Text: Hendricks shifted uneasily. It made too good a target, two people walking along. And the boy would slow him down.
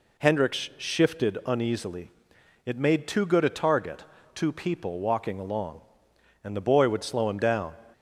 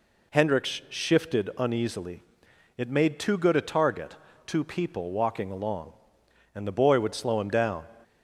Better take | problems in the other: neither | none

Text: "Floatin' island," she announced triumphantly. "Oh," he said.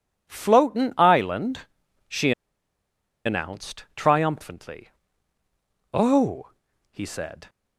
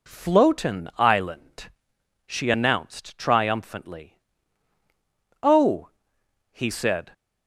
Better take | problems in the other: second | pauses between "she" and "announced"; noticeable; at 2.3 s; 0.92 s long

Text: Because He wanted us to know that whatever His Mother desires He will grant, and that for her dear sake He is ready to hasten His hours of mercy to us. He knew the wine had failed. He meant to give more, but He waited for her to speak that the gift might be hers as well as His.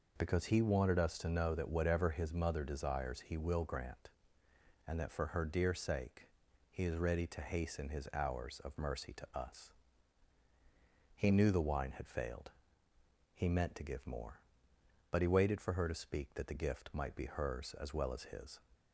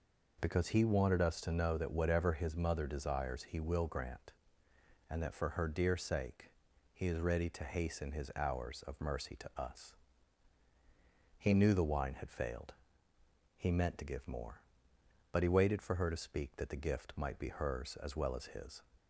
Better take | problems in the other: neither | pauses between "sake" and "He"; the same in both

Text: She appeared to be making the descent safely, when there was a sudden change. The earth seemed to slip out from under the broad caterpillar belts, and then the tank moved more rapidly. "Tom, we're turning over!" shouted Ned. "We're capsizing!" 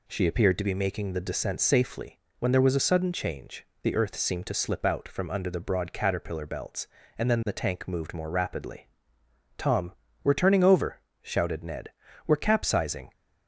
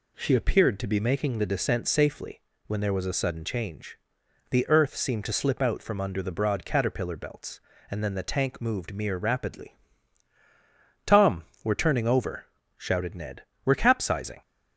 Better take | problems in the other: first | says "mere" for "more"; at 8.9 s

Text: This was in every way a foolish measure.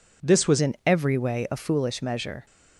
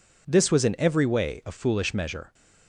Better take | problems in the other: second | changes voice at "in"; from 0.6 s on; 1.8 s long

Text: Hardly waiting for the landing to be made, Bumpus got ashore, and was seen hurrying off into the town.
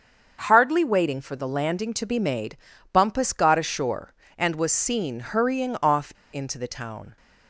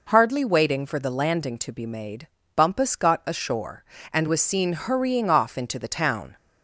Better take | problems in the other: second | starts louder than the rest; until 1.4 s; 6.5 dB // pauses between "off" and "into"; slight; at 6.1 s; 0.19 s long

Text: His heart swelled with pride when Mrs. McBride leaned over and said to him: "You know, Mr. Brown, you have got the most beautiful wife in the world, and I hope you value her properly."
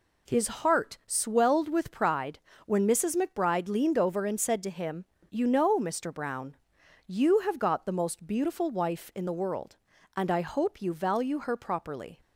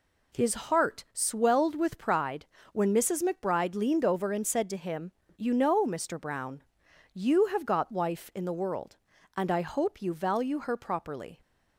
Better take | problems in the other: first | pauses between "pride" and "when"; slight; at 2.4 s; 0.26 s long; slight in the first // skips "the most beautiful"; at 7.9 s

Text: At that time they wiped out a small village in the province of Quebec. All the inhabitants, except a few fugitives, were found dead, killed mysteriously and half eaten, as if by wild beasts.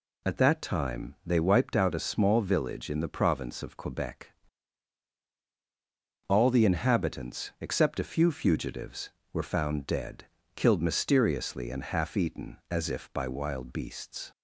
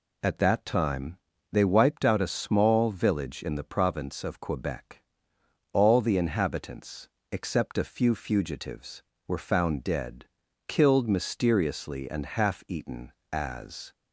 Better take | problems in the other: first | pauses between "time" and "they"; slight; at 1.1 s; 0.34 s long // stops before "if by wild beasts"; at 13.9 s

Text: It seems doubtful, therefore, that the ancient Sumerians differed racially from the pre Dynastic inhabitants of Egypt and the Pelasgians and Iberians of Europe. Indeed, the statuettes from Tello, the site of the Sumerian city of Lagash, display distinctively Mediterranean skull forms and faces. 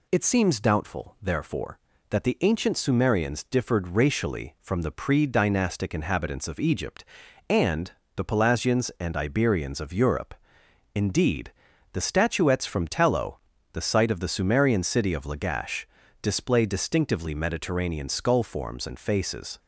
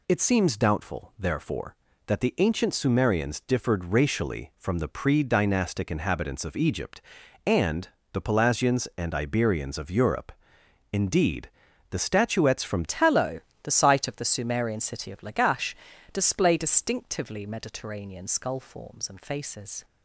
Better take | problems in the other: first | pauses between "and" and "the"; slight; at 7.8 s; 0.24 s long; slight in the first // changes voice at "Tello"; from 12.8 s on; 7.0 s long

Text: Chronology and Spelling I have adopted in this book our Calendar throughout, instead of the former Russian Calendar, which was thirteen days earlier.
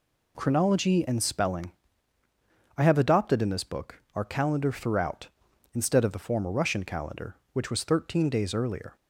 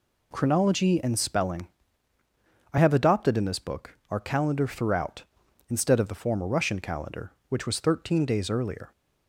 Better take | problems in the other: neither | pauses between "Spelling" and "I"; the same in both

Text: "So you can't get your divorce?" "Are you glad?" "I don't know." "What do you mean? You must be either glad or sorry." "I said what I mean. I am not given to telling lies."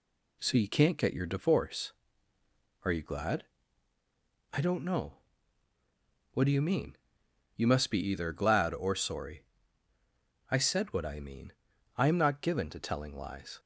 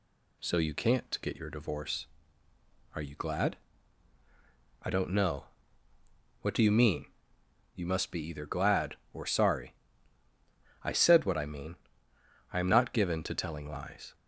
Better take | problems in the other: second | gets quieter; slight; throughout; 3.5 dB

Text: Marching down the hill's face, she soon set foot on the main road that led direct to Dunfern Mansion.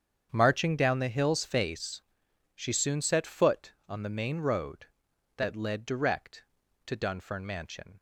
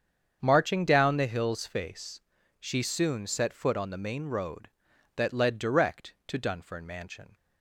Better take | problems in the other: neither | starts louder than the rest; strong; the same in both

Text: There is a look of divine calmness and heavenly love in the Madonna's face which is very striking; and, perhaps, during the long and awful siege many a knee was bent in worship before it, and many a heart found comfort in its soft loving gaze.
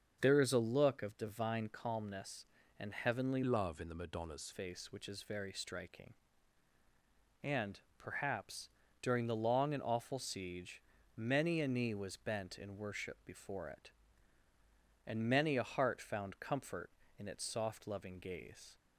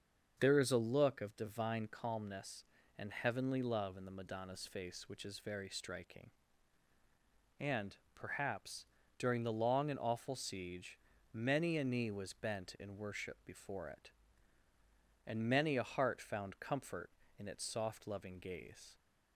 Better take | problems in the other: second | starts louder than the rest; until 1.2 s; 6.5 dB; also in the second // changes voice from "love" to "Madonna's"; from 3.4 to 4.5 s; 1.1 s long // pauses between "siege" and "many"; slight; at 10.7 s; 0.36 s long; slight in the second

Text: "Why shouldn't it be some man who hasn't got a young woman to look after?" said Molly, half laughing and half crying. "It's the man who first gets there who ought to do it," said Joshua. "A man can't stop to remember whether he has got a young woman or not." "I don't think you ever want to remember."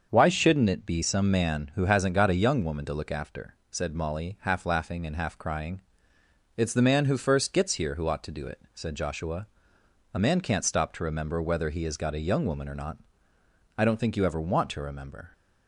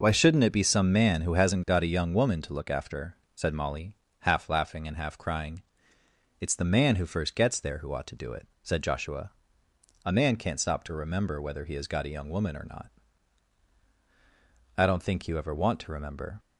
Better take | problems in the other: second | starts louder than the rest; until 1.1 s; 6.5 dB // says "here" for "there"; at 7.7 s

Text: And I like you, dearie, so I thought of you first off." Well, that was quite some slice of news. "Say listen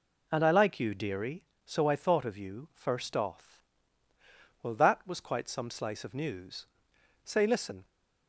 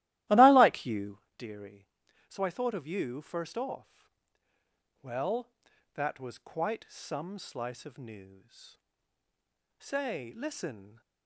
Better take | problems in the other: first | starts louder than the rest; strong; until 1.3 s; 15.5 dB

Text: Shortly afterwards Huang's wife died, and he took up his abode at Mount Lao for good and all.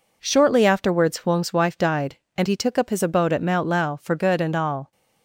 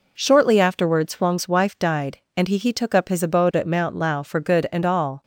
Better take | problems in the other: first | says "he" twice; at 2.5 s

